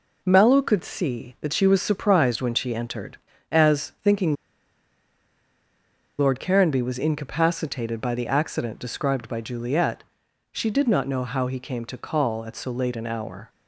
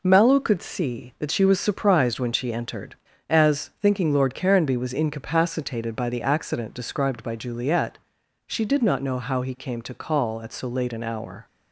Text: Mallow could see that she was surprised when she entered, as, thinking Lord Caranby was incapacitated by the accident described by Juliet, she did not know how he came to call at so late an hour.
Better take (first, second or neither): second